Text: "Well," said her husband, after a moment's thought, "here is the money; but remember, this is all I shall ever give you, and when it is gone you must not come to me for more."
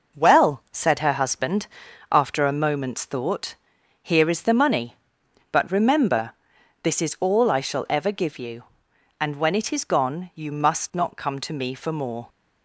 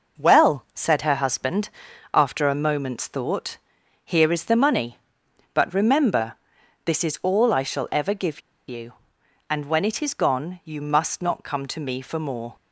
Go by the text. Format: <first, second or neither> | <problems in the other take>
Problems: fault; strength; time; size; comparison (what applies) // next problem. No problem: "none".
first | pauses between "give" and "you"; slight; at 8.4 s; 0.27 s long